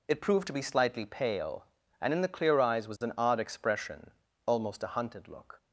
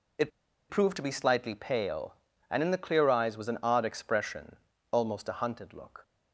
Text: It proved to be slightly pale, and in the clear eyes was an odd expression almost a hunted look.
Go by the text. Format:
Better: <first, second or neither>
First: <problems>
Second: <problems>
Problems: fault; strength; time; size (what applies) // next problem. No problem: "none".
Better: first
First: pauses between "expression" and "almost"; slight; at 4.1 s; 0.36 s long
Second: pauses between "It" and "proved"; at 0.2 s; 0.40 s long // pauses between "expression" and "almost"; slight; at 4.5 s; 0.36 s long